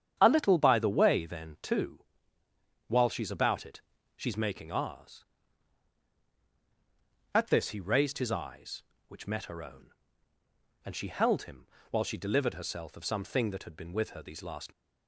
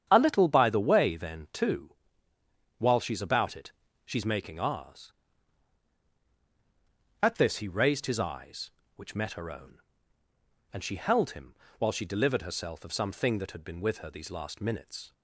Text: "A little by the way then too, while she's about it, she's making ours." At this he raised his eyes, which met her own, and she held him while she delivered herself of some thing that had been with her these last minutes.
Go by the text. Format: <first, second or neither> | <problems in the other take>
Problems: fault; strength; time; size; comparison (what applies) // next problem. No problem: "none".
second | starts louder than the rest; strong; until 1.2 s; 9 dB; strong in the second // pauses between "him" and "while"; slight; at 11.6 s; 0.24 s long; slight in the second // stops before "minutes"; at 14.7 s